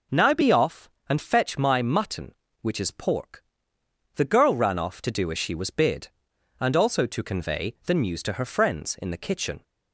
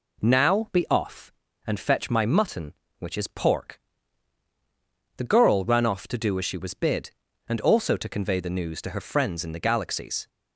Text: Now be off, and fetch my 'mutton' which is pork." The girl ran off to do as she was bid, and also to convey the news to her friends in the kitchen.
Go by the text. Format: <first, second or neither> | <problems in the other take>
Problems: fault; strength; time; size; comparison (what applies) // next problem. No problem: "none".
first | says "galaxies" for "kitchen"; at 9.6 s